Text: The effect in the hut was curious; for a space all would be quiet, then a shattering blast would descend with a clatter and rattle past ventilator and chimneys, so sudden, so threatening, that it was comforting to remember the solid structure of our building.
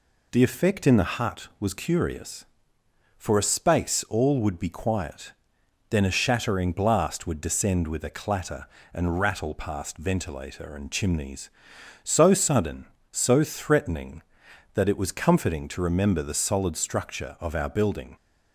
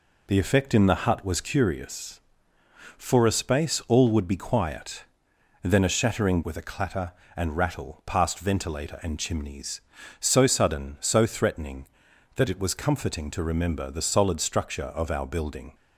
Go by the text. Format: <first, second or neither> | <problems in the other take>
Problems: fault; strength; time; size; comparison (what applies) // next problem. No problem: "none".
first | skips "blast would descend"; at 6.4 s